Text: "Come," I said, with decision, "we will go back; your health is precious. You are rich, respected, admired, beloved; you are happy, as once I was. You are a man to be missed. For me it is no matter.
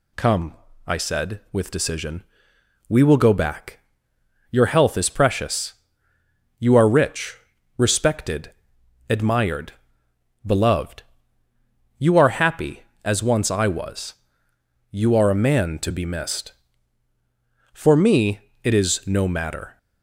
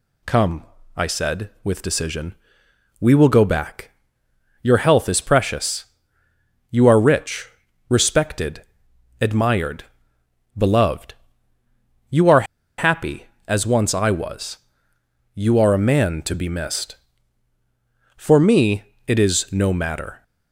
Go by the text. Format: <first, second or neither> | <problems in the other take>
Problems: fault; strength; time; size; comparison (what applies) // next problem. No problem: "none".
first | pauses between "are" and "happy"; slight; at 12.4 s; 0.34 s long // pauses between "me" and "it"; slight; at 18.8 s; 0.24 s long; slight in the first